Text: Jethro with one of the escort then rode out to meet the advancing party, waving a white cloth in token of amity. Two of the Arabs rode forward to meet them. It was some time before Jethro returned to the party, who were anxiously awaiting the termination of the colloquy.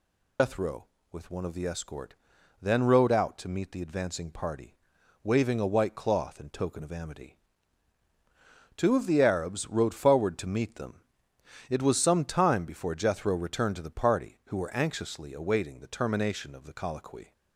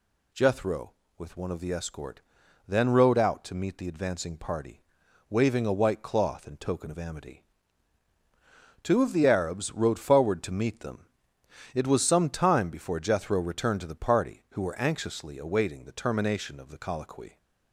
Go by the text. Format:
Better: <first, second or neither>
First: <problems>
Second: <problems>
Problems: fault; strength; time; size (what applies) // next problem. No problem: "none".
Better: second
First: loses the start of "Jethro"; at 0.3 s; 125 ms // pauses between "escort" and "then"; noticeable; at 2.1 s; 0.46 s long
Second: pauses between "escort" and "then"; noticeable; at 2.2 s; 0.46 s long